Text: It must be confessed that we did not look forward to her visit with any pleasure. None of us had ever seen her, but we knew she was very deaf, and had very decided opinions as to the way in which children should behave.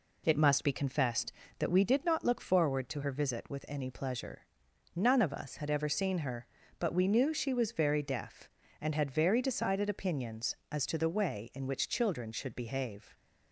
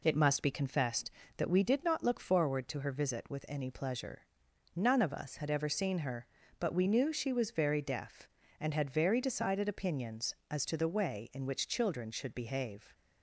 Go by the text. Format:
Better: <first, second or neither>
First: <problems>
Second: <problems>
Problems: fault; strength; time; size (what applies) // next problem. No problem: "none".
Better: neither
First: none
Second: none